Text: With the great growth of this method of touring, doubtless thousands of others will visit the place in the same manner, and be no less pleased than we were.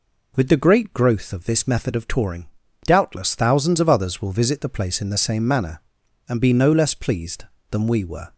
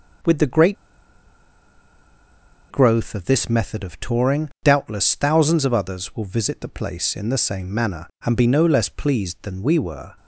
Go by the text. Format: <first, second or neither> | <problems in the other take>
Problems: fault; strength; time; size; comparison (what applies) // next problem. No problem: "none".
first | pauses between "great" and "growth"; strong; at 0.7 s; 1.9 s long